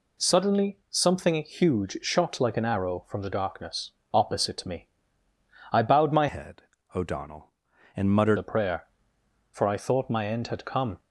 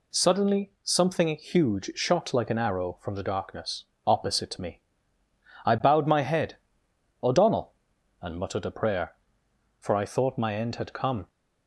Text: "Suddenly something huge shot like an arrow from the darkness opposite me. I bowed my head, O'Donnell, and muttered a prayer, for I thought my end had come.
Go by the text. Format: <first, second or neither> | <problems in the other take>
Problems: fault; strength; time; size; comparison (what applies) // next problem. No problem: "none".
second | pauses between "darkness" and "opposite"; slight; at 3.9 s; 0.20 s long; slight in the second // changes voice from "head" to "muttered"; from 6.2 to 8.3 s; 2.1 s long